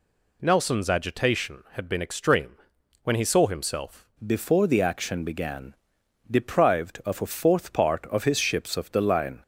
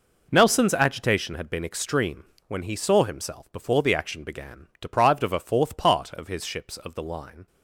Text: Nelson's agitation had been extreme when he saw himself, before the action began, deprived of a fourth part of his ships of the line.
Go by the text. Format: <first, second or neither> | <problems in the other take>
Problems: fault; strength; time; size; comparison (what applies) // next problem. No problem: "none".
second | pauses between "extreme" and "when"; noticeable; at 2.5 s; 0.48 s long; slight in the second // changes voice at "before"; from 4.2 s on; 5.2 s long